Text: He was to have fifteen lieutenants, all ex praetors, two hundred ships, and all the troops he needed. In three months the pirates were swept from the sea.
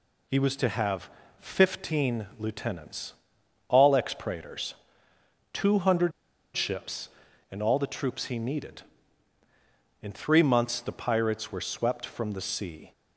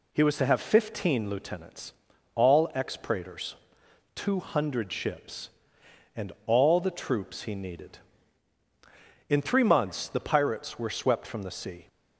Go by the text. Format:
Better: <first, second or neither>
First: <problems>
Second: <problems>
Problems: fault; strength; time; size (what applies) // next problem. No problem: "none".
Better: second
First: pauses between "have" and "fifteen"; slight; at 1.0 s; 0.30 s long // pauses between "hundred" and "ships"; at 6.1 s; 0.44 s long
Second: none